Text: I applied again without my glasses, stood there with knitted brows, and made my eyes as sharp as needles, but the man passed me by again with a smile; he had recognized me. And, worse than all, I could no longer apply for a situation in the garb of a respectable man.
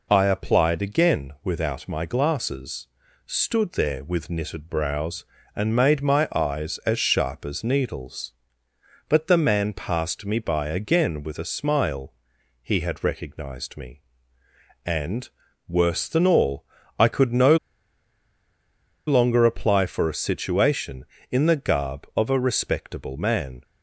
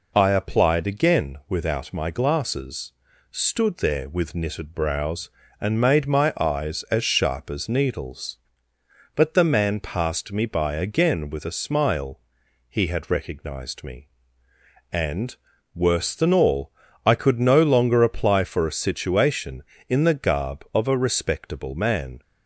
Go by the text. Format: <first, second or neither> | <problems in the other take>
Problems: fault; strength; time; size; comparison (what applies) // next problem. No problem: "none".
second | pauses between "no" and "longer"; strong; at 17.5 s; 1.5 s long